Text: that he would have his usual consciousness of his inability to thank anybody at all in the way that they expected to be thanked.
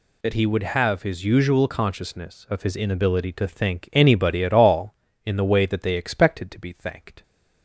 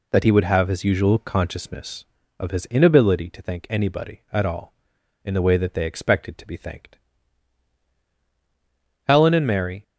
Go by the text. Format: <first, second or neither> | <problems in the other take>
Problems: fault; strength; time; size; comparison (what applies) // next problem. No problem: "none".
first | goes on to say "Helen and Mary"; noticeable; from 9.0 s on; 0.76 s long